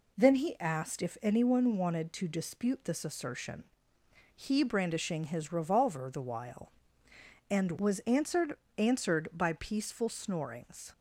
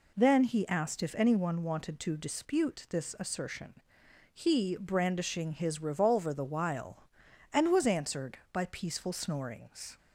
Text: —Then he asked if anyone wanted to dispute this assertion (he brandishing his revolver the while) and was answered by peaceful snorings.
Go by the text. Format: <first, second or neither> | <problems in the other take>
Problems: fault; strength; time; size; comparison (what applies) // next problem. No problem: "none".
second | says "answered" twice; at 8.7 s